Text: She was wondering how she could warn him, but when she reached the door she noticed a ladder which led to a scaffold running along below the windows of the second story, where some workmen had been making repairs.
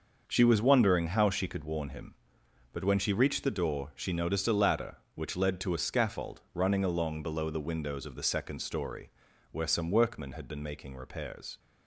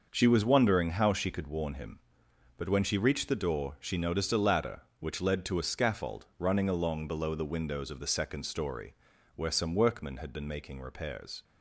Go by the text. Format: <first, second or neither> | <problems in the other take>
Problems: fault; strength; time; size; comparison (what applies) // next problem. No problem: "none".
neither | starts louder than the rest; noticeable; the same in both